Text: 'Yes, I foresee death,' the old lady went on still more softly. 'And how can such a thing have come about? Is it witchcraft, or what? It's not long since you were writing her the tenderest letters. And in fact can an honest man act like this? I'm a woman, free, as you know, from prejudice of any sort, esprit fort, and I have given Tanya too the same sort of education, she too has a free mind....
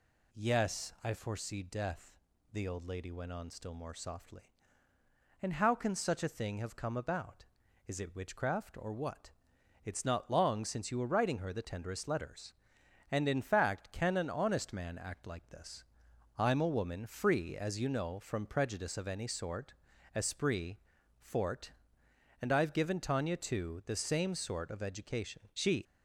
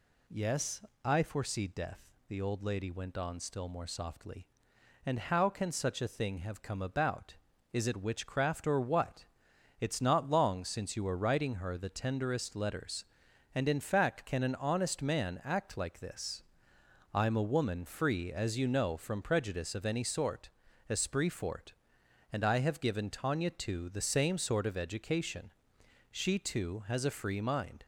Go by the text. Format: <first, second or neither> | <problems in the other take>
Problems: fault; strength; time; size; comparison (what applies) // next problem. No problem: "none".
second | pauses between "esprit" and "fort"; at 20.7 s; 0.44 s long // stops before "too has a free mind"; at 25.8 s